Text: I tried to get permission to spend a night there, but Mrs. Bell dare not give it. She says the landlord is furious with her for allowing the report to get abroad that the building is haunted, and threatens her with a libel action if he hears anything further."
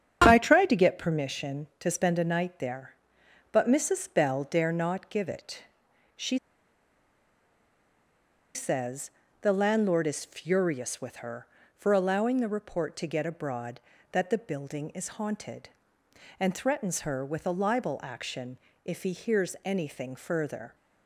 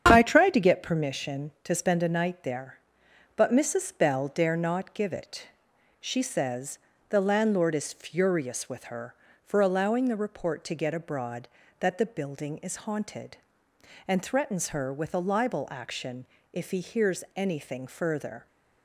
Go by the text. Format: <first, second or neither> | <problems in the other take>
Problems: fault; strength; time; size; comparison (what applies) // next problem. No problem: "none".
second | starts louder than the rest; strong; until 1.2 s; 8 dB; strong in the second // pauses between "She" and "says"; strong; at 6.3 s; 2.1 s long // pauses between "says" and "the"; slight; at 9.1 s; 0.30 s long; slight in the second // pauses between "action" and "if"; slight; at 18.5 s; 0.28 s long; slight in the second